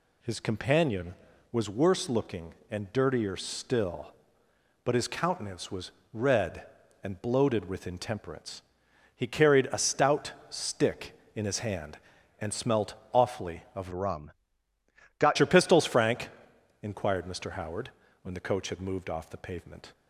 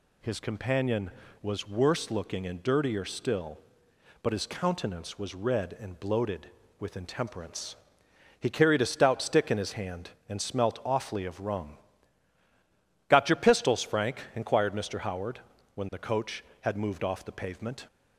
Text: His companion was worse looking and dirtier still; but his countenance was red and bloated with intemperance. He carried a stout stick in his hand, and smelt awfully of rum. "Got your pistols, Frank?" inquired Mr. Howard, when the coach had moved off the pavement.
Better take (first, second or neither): second